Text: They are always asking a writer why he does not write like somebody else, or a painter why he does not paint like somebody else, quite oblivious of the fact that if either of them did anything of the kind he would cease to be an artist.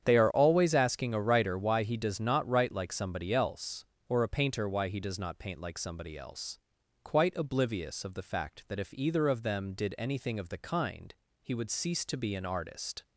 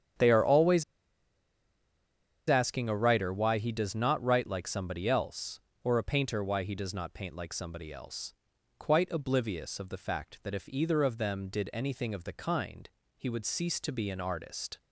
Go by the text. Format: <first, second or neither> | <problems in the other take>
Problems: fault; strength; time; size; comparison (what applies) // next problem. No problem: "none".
first | starts louder than the rest; strong; until 2.8 s; 8.5 dB; strong in the first // pauses between "always" and "asking"; strong; at 0.8 s; 1.6 s long // pauses between "kind" and "he"; slight; at 12.8 s; 0.28 s long; slight in the first